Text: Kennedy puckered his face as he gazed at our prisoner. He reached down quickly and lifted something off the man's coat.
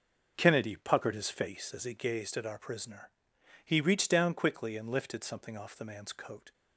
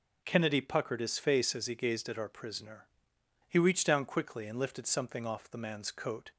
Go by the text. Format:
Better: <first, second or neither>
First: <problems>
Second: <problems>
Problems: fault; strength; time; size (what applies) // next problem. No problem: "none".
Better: second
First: starts louder than the rest; until 1.6 s; 6 dB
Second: none